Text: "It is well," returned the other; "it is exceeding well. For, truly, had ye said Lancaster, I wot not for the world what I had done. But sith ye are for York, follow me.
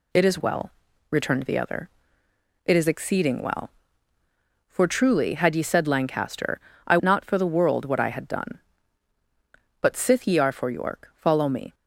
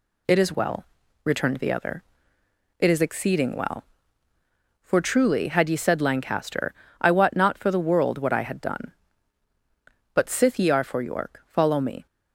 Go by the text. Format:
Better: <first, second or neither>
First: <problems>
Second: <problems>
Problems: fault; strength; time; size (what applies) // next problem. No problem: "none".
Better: second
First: skips "wot"; at 6.9 s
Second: none